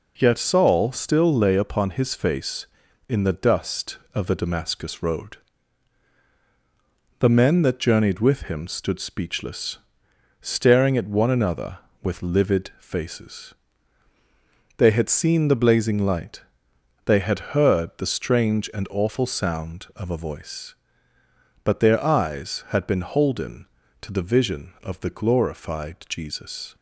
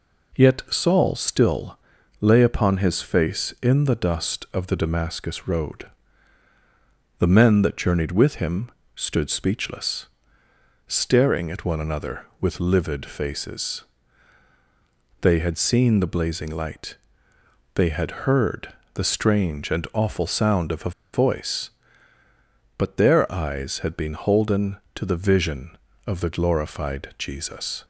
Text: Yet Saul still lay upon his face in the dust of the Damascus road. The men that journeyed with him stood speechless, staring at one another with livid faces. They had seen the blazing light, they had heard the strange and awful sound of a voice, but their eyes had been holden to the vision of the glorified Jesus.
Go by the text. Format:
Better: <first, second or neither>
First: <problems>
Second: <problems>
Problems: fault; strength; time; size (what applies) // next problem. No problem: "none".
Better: first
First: none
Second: pauses between "still" and "lay"; at 1.7 s; 0.42 s long // pauses between "him" and "stood"; slight; at 8.7 s; 0.24 s long // pauses between "heard" and "the"; slight; at 18.6 s; 0.24 s long // pauses between "a" and "voice"; slight; at 20.9 s; 0.22 s long